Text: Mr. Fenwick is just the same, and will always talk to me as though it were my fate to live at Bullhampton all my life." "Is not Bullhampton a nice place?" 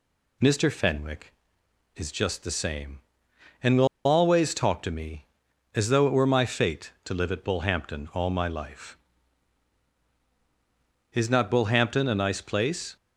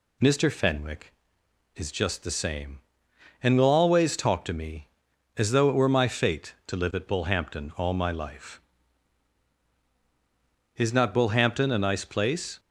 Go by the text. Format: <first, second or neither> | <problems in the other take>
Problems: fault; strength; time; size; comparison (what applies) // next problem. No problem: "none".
second | pauses between "will" and "always"; slight; at 3.8 s; 0.18 s long